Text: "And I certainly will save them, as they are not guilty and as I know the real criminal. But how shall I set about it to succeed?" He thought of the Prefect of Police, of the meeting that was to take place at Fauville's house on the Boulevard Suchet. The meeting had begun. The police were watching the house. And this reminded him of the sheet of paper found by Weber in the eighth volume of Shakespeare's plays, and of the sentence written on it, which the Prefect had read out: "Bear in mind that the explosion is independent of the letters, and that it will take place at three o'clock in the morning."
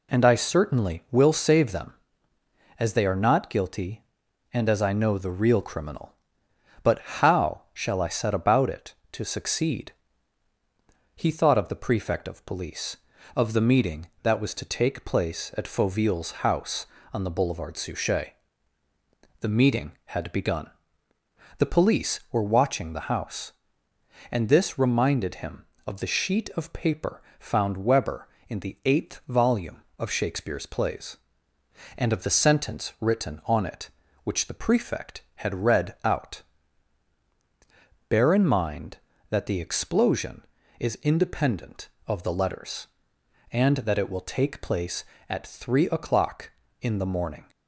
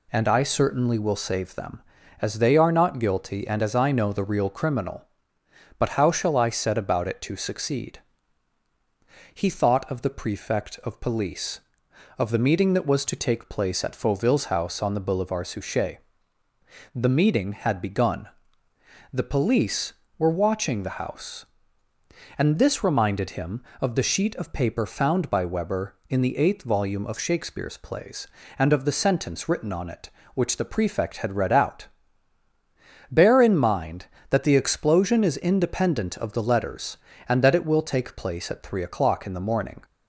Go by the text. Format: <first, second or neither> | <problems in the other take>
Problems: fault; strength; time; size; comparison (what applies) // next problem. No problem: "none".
second | pauses between "paper" and "found"; slight; at 27.2 s; 0.16 s long // skips "by"; at 27.8 s